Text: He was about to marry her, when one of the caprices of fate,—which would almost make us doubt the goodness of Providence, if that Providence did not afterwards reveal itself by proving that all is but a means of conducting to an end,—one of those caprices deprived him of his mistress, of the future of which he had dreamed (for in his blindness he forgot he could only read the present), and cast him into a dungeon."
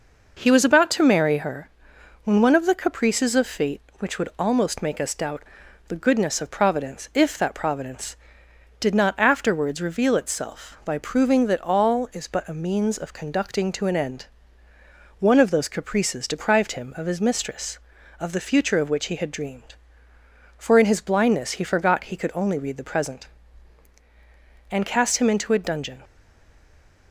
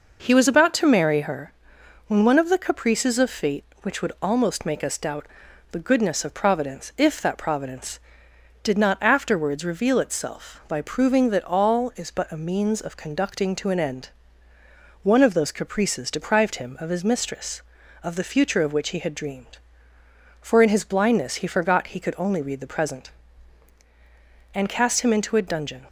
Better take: second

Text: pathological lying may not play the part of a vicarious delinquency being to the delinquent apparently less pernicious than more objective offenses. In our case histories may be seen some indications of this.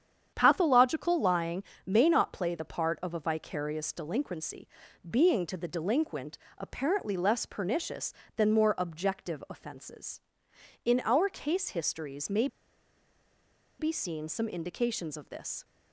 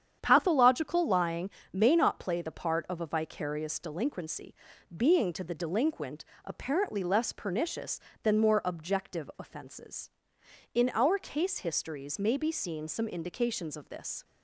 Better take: second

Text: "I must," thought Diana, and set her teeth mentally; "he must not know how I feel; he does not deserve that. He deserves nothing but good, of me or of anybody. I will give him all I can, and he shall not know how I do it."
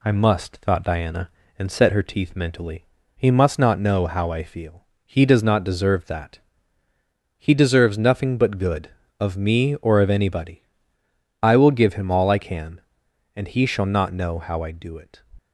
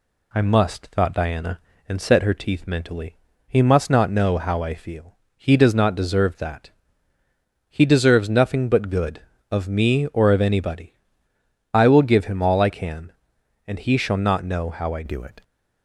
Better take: first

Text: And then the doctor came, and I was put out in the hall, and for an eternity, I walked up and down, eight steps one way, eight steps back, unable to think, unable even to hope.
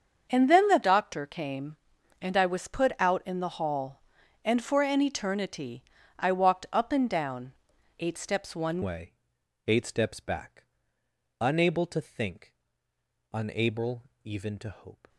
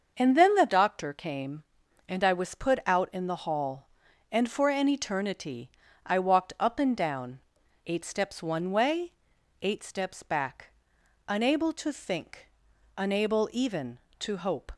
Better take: second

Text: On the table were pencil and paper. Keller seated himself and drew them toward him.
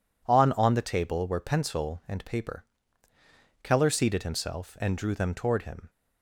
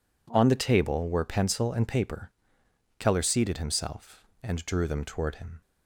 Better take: second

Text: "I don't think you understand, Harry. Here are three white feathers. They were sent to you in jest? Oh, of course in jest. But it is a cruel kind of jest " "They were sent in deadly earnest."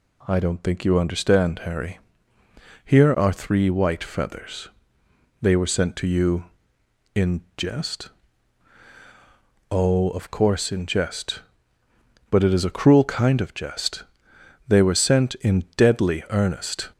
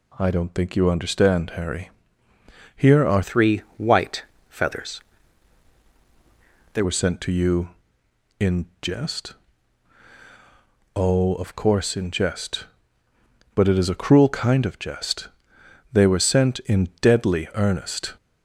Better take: first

